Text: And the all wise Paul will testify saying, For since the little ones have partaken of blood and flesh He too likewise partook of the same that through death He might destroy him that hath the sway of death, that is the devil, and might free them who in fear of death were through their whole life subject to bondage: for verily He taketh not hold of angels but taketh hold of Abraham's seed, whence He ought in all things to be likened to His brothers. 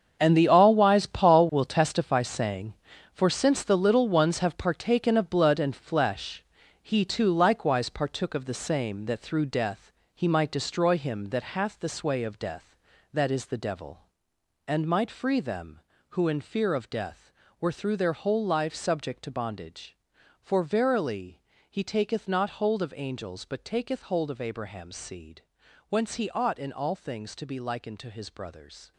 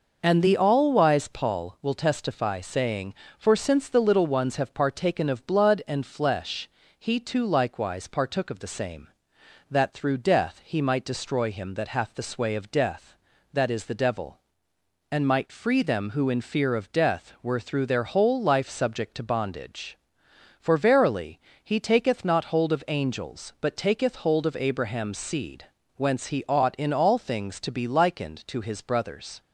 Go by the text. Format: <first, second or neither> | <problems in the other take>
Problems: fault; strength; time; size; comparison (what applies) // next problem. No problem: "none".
second | gets quieter; strong; throughout; 12 dB // pauses between "flesh" and "He"; at 6.4 s; 0.40 s long; slight in the second // pauses between "death" and "He"; slight; at 9.9 s; 0.22 s long // pauses between "verily" and "He"; slight; at 21.4 s; 0.26 s long; slight in the second